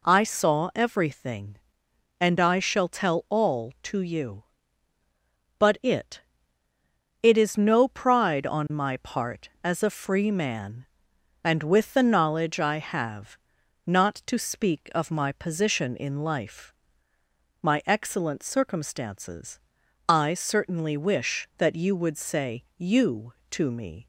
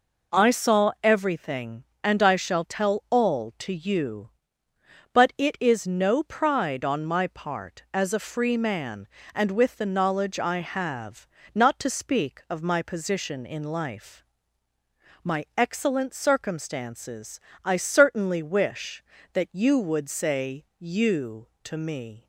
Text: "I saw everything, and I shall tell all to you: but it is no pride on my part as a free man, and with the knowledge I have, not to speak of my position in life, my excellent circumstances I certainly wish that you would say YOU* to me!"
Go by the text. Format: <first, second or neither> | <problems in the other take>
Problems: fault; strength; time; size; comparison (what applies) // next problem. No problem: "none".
second | says "it" twice; at 7.2 s // pauses between "circumstances" and "I"; noticeable; at 19.5 s; 0.50 s long; slight in the second // pauses between "say" and "YOU"; slight; at 22.6 s; 0.16 s long; slight in the second